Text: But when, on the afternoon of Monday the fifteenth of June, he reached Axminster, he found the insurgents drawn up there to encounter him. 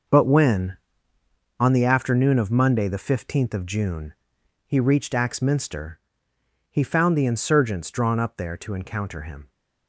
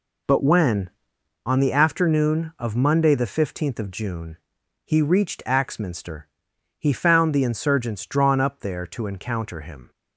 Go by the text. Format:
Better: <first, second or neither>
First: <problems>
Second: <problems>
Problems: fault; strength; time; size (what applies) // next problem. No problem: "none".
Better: second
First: gets quieter; strong; throughout; 10 dB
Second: none